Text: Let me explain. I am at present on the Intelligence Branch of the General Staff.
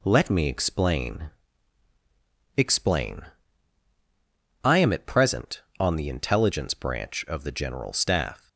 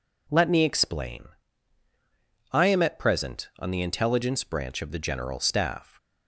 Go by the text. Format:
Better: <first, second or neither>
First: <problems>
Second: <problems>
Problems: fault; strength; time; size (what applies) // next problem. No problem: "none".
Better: second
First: says "explain" twice; at 2.5 s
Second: none